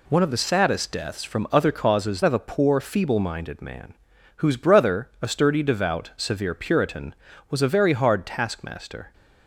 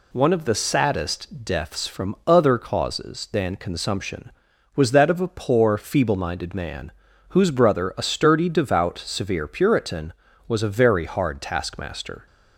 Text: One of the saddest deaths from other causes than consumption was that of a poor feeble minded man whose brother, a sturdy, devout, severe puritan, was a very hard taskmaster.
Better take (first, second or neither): second